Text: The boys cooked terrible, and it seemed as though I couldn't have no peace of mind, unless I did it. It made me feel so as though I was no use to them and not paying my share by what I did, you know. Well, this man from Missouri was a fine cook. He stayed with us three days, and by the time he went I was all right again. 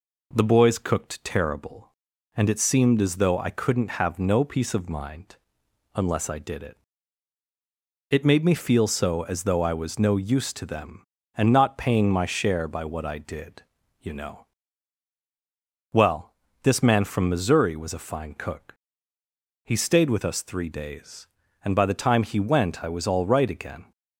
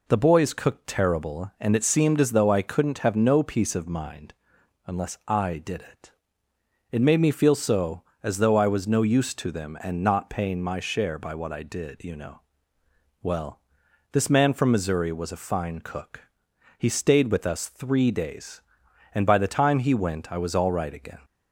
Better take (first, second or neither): neither